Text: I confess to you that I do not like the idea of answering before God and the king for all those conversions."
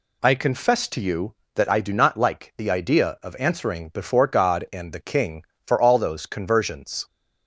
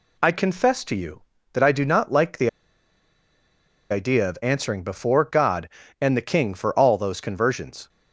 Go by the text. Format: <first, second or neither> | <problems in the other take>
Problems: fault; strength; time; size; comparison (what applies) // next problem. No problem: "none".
first | pauses between "the" and "idea"; strong; at 2.4 s; 1.4 s long